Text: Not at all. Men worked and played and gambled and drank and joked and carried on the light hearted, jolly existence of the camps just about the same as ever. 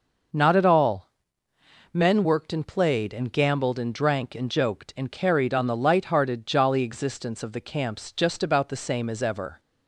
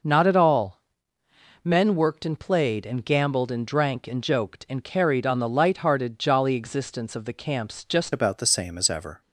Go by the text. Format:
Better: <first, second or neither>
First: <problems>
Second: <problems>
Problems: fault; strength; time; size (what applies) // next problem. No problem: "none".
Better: first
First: none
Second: changes voice at "about"; from 8.1 s on; 1.1 s long